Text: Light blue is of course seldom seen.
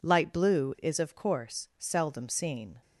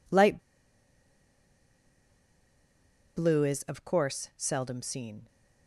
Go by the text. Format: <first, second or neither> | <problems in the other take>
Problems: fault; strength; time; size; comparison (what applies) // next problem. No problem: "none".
first | pauses between "Light" and "blue"; strong; at 0.3 s; 2.7 s long